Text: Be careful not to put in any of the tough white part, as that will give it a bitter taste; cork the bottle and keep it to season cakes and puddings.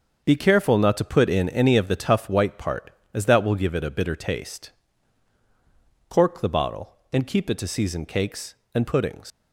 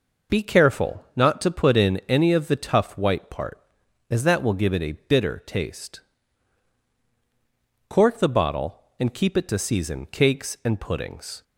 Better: second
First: starts louder than the rest; until 1.2 s; 6.5 dB // leaves "puddings" unfinished; at 9.3 s; 105 ms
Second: none

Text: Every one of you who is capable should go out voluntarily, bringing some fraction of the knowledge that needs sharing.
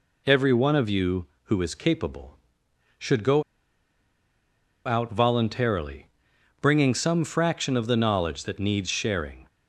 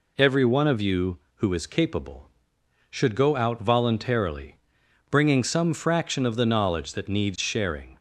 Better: second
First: pauses between "go" and "out"; strong; at 3.4 s; 1.4 s long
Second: none

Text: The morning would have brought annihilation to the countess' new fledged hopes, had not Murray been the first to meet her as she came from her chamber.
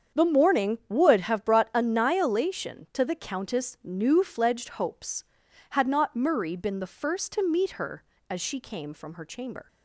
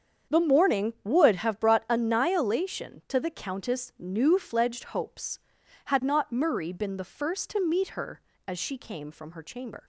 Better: neither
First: starts louder than the rest; strong; until 1.2 s; 7.5 dB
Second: starts louder than the rest; strong; until 1.4 s; 7.5 dB

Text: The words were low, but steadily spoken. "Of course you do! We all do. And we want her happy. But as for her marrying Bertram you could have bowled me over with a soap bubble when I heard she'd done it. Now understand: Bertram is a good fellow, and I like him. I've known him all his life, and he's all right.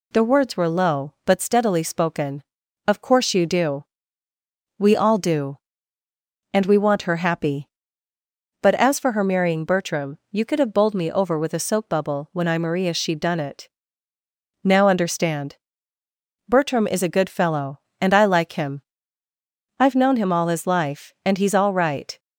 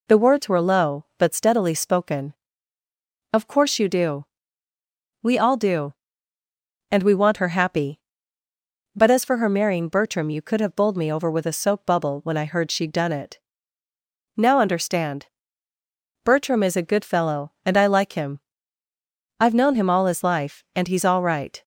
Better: second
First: says "maria" for "heard"; at 12.5 s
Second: none

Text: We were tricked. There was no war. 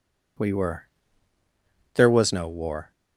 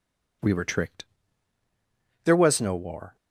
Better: second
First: skips "tricked"; at 1.4 s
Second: none

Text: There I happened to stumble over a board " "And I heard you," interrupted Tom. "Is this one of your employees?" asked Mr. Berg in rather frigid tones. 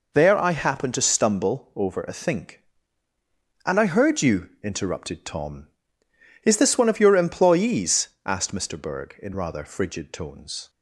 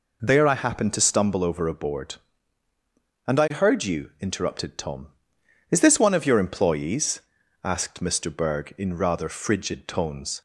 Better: second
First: says "think" for "board"; at 2.1 s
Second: none

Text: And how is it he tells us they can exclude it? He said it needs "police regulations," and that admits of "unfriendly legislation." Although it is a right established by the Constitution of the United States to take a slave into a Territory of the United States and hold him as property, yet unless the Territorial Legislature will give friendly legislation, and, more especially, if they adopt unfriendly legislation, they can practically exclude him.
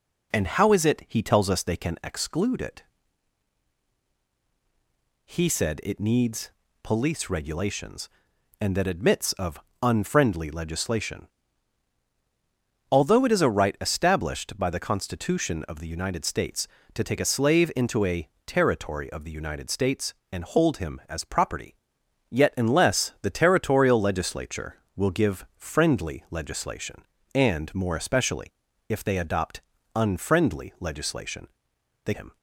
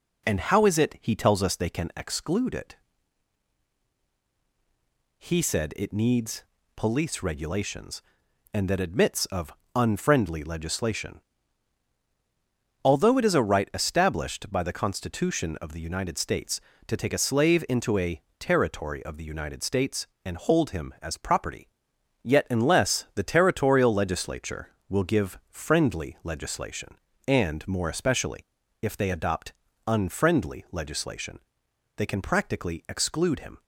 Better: second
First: pauses between "needs" and "police"; slight; at 6.4 s; 0.34 s long // pauses between "of" and "unfriendly"; slight; at 9.6 s; 0.20 s long // pauses between "a" and "Territory"; slight; at 18.2 s; 0.18 s long // pauses between "adopt" and "unfriendly"; slight; at 29.6 s; 0.34 s long // skips "can practically exclude"; at 32.1 s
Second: pauses between "needs" and "police"; slight; at 6.4 s; 0.34 s long // pauses between "of" and "unfriendly"; slight; at 9.5 s; 0.20 s long // pauses between "a" and "Territory"; slight; at 18.2 s; 0.18 s long // pauses between "adopt" and "unfriendly"; slight; at 29.5 s; 0.34 s long

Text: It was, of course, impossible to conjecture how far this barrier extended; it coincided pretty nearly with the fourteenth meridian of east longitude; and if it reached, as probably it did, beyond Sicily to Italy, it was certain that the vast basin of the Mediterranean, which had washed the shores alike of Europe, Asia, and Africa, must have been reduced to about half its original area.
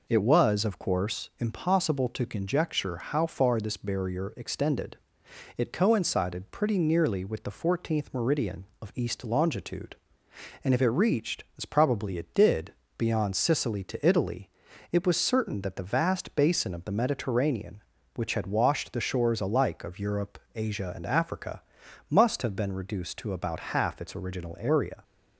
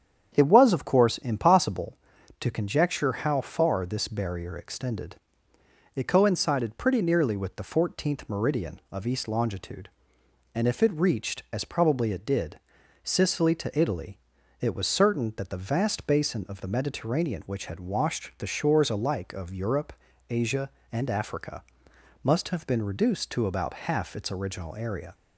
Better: first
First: none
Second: starts louder than the rest; strong; until 1.3 s; 8.5 dB // skips "beyond"; at 12.8 s

